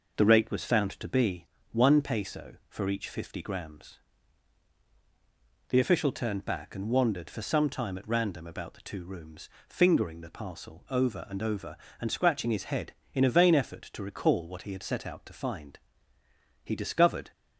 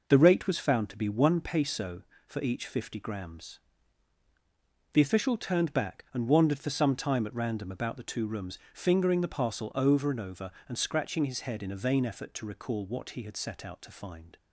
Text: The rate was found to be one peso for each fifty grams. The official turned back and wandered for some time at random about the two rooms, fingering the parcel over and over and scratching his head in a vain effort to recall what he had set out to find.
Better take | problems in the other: second | pauses between "be" and "one"; slight; at 1.4 s; 0.24 s long // goes on to say "He discovered"; noticeable; from 16.6 s on; 0.68 s long

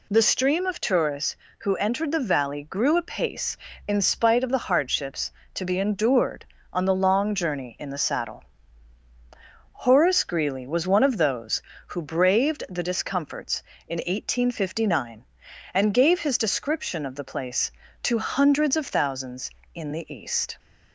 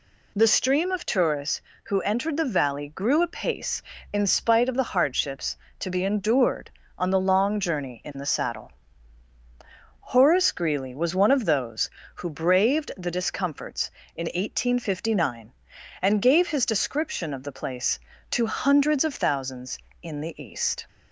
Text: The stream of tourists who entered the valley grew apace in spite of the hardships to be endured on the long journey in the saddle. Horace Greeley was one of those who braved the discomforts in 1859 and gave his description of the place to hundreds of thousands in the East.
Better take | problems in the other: neither | none

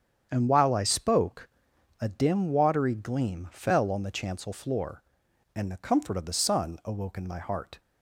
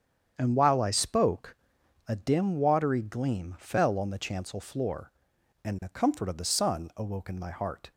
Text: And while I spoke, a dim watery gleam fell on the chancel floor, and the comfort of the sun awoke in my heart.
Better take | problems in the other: neither | starts louder than the rest; strong; the same in both

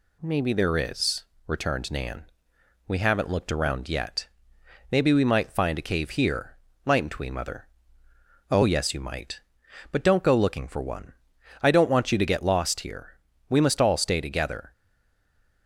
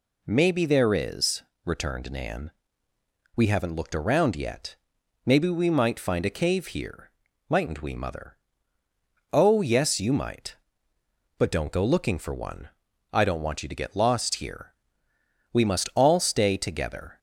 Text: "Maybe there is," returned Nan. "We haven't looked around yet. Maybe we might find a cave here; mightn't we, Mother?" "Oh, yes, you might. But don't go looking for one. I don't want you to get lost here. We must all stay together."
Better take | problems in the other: second | stays silent after the last word; slight; from 14.7 s on; 0.9 s long

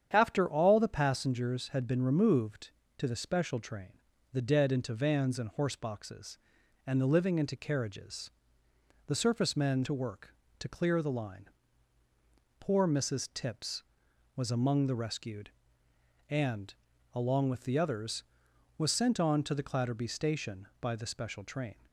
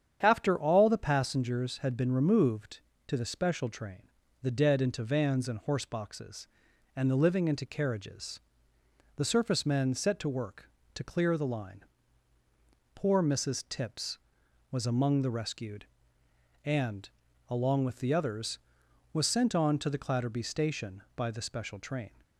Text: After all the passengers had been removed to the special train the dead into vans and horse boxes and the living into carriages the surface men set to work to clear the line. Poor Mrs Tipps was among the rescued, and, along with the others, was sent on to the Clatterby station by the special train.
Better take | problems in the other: second | starts louder than the rest; strong; until 1.1 s; 8.5 dB; strong in the second // pauses between "train" and "the"; at 3.9 s; 0.40 s long; also in the second // pauses between "carriages" and "the"; noticeable; at 8.2 s; 0.76 s long; noticeable in the second // skips "set"; at 9.8 s

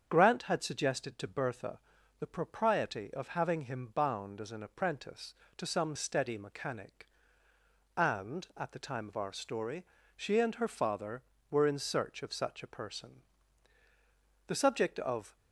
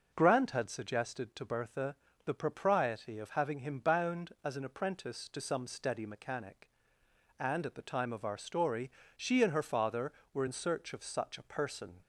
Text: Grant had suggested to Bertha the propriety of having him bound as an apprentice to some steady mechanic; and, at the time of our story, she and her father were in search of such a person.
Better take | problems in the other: second | starts louder than the rest; strong; until 1.0 s; 7.5 dB // pauses between "Bertha" and "the"; at 1.7 s; 0.40 s long; slight in the second // goes on to say "The subject of"; noticeable; from 14.4 s on; 0.90 s long

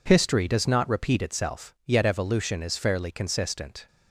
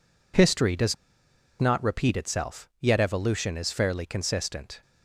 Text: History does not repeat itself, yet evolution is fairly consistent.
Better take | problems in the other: first | pauses between "does" and "not"; noticeable; at 0.9 s; 0.66 s long

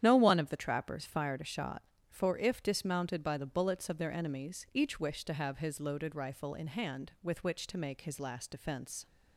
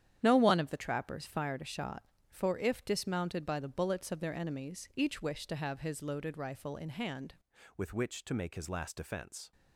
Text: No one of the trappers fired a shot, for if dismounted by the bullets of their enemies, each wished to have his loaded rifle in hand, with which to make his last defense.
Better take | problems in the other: first | starts louder than the rest; strong; until 1.2 s; 10 dB; strong in the first // changes voice at "with"; from 7.7 s on; 1.8 s long

